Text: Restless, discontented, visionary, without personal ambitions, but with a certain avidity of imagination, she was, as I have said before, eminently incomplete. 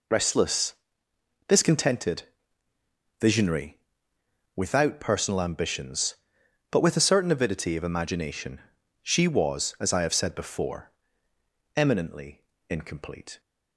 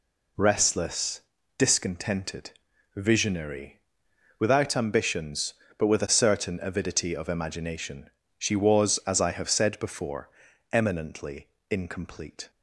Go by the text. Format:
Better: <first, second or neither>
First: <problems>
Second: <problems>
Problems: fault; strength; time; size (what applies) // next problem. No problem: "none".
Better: first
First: pauses between "eminently" and "incomplete"; slight; at 12.3 s; 0.30 s long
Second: skips "personal"; at 4.7 s // pauses between "eminently" and "incomplete"; slight; at 11.4 s; 0.22 s long